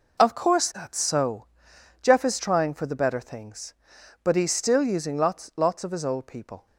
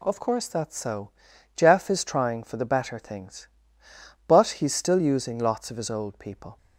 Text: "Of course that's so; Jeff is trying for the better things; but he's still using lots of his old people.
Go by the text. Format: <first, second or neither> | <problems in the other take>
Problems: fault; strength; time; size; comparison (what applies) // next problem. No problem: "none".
second | says "lots" twice; at 5.5 s